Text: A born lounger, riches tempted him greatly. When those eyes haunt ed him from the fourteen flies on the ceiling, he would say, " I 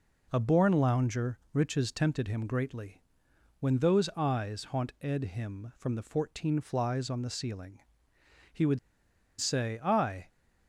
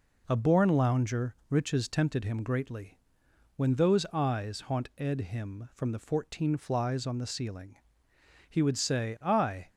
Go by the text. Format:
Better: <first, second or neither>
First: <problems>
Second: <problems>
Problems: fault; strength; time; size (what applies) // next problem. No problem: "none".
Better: second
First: pauses between "would" and "say"; noticeable; at 8.7 s; 0.61 s long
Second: none